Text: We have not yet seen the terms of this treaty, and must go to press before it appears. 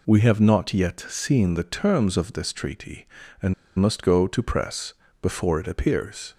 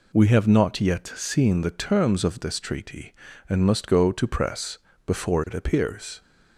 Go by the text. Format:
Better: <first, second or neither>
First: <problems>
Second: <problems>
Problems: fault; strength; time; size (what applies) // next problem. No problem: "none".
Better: second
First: pauses between "and" and "must"; slight; at 3.5 s; 0.25 s long // pauses between "press" and "before"; slight; at 4.9 s; 0.30 s long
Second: pauses between "press" and "before"; slight; at 4.7 s; 0.30 s long